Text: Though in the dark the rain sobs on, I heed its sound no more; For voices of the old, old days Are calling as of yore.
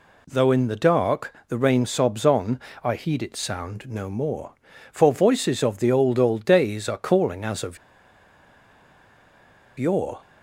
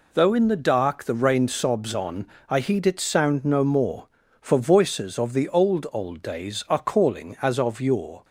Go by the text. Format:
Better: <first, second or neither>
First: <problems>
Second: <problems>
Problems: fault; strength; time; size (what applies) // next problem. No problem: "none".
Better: second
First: pauses between "dark" and "the"; slight; at 1.3 s; 0.16 s long // pauses between "of" and "yore"; strong; at 7.7 s; 2.0 s long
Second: none